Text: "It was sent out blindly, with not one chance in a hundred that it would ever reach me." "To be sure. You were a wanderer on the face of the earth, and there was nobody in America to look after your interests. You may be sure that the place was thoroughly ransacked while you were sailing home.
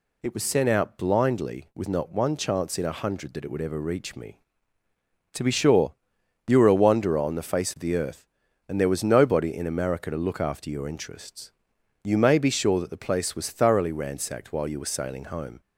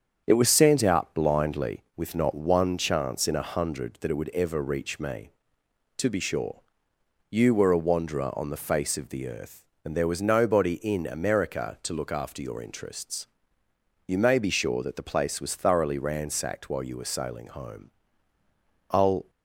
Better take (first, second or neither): first